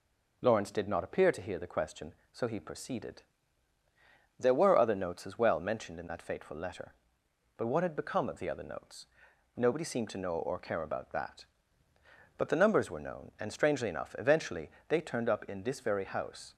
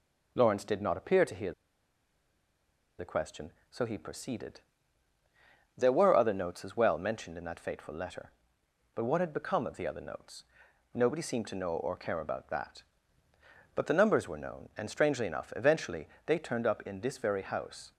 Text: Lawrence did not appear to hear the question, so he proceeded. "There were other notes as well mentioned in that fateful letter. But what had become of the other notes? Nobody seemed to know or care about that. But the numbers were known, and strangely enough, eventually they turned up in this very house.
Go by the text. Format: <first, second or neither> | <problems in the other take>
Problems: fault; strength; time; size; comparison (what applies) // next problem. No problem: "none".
first | pauses between "hear" and "the"; strong; at 1.5 s; 1.4 s long // pauses between "eventually" and "they"; slight; at 16.0 s; 0.18 s long; slight in the first